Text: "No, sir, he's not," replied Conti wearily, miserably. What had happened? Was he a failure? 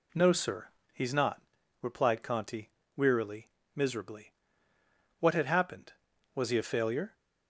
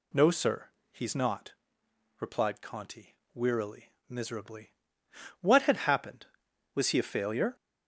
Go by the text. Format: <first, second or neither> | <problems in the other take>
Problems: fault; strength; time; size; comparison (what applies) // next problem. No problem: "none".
first | gets louder; noticeable; throughout; 4 dB // pauses between "Conti" and "wearily"; slight; at 3.1 s; 0.18 s long; slight in the first